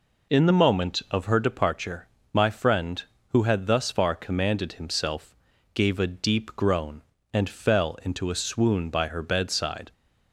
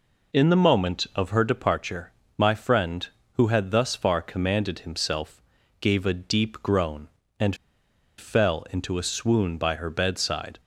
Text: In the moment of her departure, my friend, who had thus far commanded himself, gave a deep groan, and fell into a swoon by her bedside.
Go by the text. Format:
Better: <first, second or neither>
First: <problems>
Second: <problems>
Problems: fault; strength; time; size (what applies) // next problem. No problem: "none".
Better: first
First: none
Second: pauses between "and" and "fell"; noticeable; at 7.5 s; 0.63 s long